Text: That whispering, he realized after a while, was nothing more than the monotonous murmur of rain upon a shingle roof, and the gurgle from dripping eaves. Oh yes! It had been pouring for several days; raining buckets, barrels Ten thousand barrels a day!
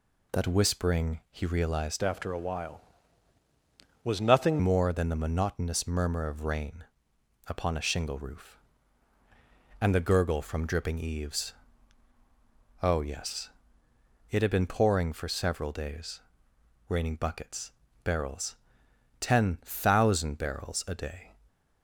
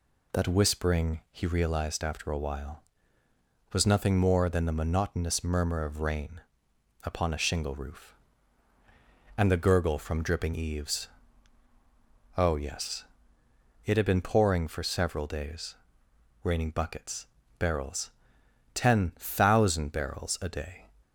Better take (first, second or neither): second